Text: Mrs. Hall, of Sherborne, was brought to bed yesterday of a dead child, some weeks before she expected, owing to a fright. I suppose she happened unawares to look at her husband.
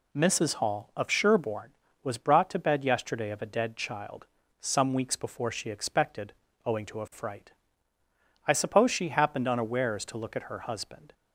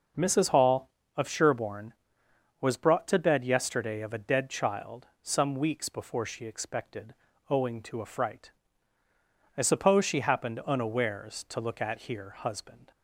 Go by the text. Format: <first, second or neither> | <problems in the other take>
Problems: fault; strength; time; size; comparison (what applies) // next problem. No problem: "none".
first | says "here" for "her"; at 12.0 s